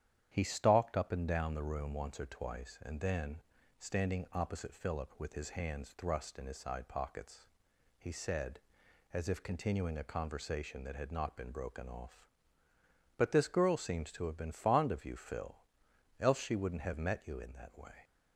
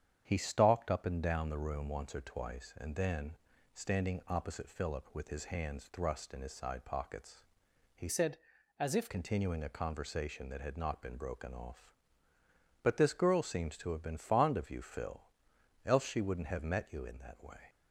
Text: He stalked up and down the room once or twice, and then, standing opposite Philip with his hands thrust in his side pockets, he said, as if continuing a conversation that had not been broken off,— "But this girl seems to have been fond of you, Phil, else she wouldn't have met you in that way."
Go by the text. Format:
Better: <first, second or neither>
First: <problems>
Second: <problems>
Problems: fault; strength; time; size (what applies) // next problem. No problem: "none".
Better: first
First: starts louder than the rest; strong; until 1.3 s; 10 dB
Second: starts louder than the rest; strong; until 1.2 s; 8.5 dB // changes voice from "said" to "if"; from 8.0 to 9.0 s; 1.0 s long